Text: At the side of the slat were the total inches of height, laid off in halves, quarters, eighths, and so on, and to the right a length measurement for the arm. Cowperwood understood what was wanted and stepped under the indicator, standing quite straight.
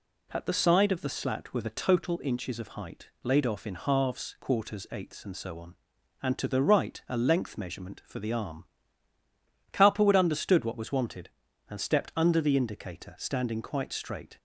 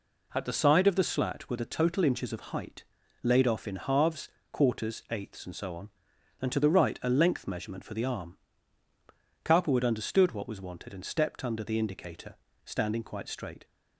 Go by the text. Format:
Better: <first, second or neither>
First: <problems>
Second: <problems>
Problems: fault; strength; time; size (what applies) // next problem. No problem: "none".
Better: neither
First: none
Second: none